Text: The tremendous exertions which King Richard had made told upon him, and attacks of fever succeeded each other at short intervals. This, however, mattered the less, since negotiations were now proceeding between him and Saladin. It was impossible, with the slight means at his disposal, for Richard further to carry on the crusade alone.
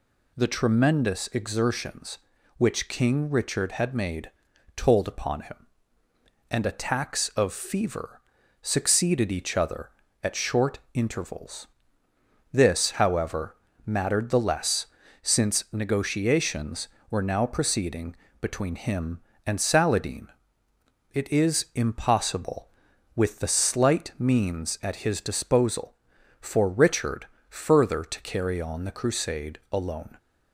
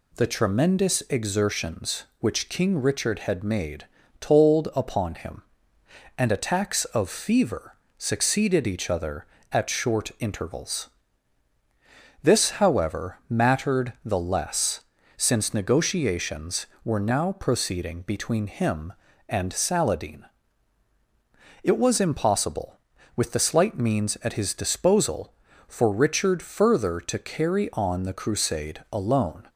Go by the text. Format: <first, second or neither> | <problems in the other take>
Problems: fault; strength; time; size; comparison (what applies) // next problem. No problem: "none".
second | pauses between "made" and "told"; at 4.3 s; 0.44 s long; slight in the second // pauses between "fever" and "succeeded"; at 8.1 s; 0.44 s long; slight in the second // pauses between "short" and "intervals"; slight; at 10.7 s; 0.16 s long // pauses between "proceeding" and "between"; slight; at 18.1 s; 0.26 s long // says "is" for "was"; at 21.3 s // pauses between "Richard" and "further"; slight; at 27.2 s; 0.24 s long